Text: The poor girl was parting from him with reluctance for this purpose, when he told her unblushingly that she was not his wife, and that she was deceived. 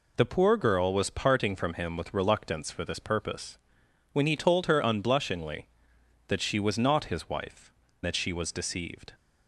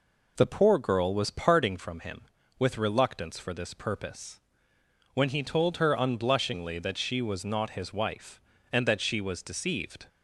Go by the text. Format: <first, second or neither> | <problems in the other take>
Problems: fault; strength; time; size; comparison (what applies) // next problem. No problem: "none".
second | skips "and"; at 7.8 s